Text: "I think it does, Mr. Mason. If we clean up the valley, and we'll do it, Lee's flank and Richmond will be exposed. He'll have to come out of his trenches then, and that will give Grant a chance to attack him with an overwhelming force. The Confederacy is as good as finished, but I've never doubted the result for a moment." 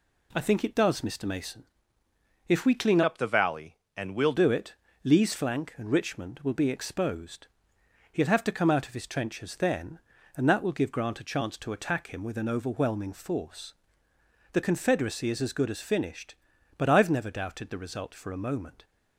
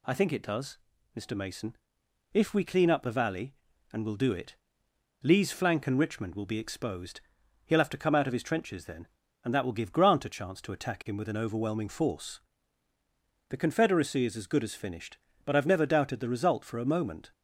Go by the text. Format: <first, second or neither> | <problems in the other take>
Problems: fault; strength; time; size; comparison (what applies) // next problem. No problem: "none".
second | changes voice from "up" to "we'll"; from 3.0 to 4.3 s; 1.3 s long